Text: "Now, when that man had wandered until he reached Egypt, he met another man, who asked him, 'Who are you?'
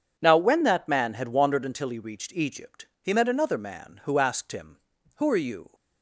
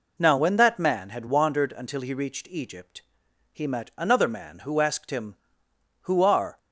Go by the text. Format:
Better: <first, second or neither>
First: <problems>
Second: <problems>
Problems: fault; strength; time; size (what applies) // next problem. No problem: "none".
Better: first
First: none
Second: stops before "you"; at 6.5 s